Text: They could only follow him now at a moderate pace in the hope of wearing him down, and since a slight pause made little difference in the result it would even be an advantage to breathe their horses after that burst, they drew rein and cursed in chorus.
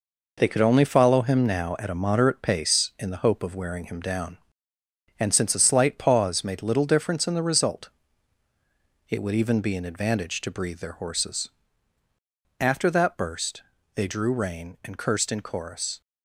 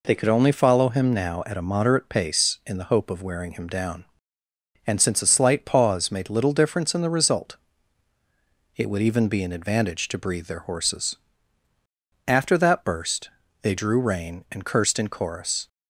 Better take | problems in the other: second | gets quieter; throughout; 7 dB // pauses between "result" and "it"; at 7.8 s; 1.2 s long; also in the second // pauses between "horses" and "after"; at 11.4 s; 1.1 s long; also in the second

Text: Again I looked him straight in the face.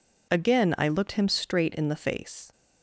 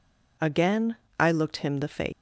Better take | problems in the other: first | pauses between "Again" and "I"; slight; at 0.9 s; 0.24 s long // skips "straight in"; at 1.7 s

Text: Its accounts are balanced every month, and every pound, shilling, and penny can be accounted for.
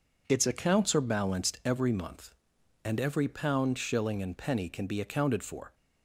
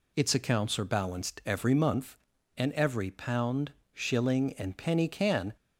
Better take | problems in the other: first | stops before "be accounted for"; at 5.5 s

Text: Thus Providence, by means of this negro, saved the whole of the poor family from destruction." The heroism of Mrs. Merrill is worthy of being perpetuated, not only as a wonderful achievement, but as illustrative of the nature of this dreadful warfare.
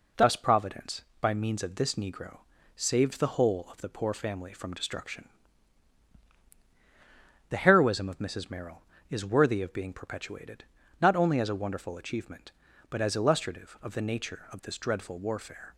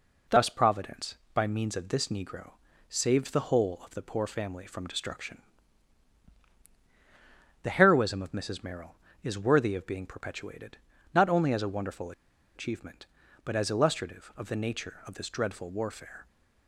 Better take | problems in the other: first | pauses between "wonderful" and "achievement"; at 12.1 s; 0.43 s long

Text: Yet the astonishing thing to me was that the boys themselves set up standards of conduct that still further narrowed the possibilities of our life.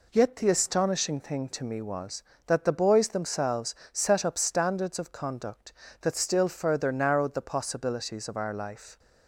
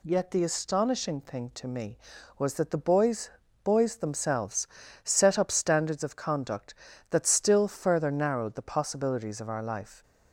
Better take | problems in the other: first | says "boys" twice; at 3.6 s // pauses between "themselves" and "set"; at 4.6 s; 0.38 s long; slight in the first

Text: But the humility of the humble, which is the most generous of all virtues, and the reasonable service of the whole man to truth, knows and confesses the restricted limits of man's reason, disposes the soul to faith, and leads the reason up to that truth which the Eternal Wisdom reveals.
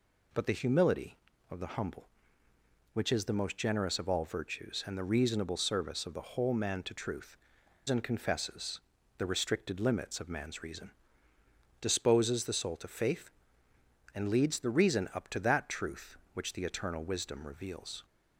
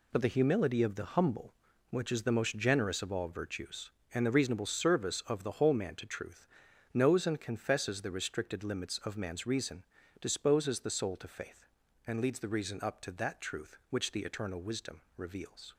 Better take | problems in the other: second | skips "knows"; at 7.6 s // pauses between "confesses" and "the"; at 8.7 s; 0.38 s long

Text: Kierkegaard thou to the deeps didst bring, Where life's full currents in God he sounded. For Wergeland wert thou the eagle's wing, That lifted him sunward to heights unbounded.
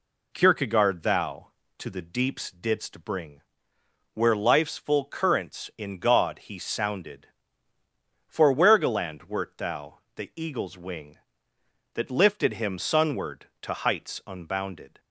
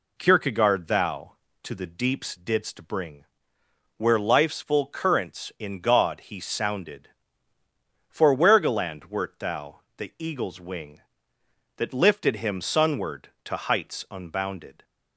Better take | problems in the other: neither | pauses between "thou" and "the"; slight; the same in both

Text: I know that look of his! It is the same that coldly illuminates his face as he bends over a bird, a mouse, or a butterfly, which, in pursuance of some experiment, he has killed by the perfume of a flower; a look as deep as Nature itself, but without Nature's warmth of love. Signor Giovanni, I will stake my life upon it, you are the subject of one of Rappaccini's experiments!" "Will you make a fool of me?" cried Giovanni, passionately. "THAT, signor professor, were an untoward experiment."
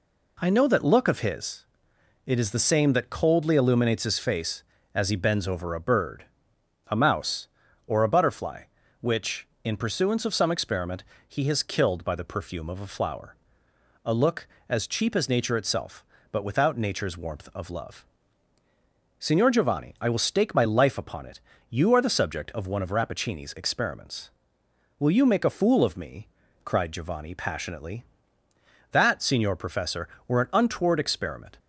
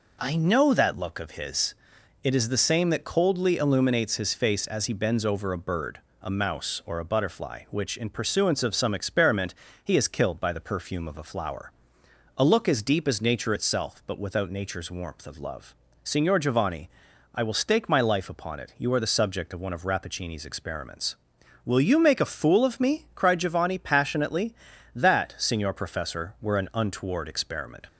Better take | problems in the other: second | says "cheap" for "deep"; at 14.8 s

